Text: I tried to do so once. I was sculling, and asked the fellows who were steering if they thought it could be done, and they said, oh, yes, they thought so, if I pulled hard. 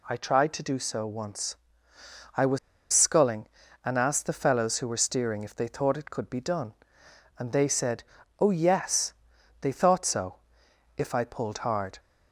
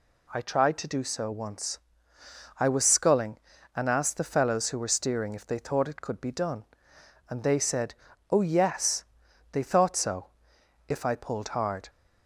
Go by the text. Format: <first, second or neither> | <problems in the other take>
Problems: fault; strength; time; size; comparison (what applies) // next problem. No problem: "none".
second | pauses between "was" and "sculling"; slight; at 2.5 s; 0.34 s long